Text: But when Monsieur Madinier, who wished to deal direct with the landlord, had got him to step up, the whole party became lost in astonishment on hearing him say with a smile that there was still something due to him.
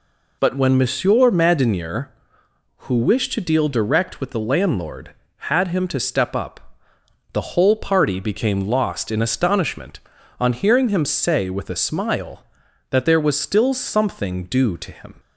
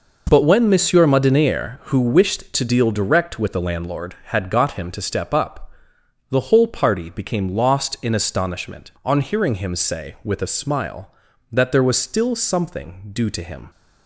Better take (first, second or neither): second